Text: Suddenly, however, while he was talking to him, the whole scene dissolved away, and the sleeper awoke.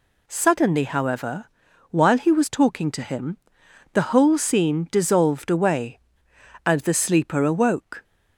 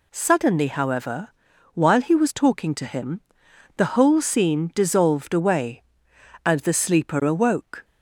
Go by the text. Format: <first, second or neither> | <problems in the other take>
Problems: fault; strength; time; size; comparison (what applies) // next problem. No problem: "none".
neither | none